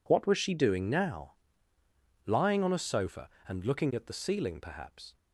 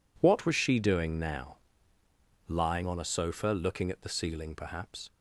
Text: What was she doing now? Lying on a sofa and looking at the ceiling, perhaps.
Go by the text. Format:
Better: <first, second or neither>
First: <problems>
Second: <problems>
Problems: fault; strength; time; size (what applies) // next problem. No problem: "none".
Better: first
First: none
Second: skips "and"; at 3.4 s